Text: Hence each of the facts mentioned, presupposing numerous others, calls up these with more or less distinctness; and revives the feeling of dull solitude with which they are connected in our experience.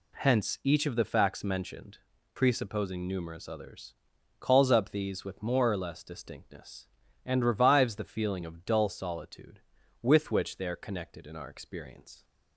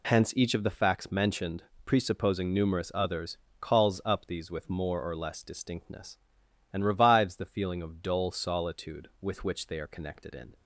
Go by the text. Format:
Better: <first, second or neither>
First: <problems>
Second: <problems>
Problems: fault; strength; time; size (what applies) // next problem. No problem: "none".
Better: first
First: none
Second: stops before "our experience"; at 10.5 s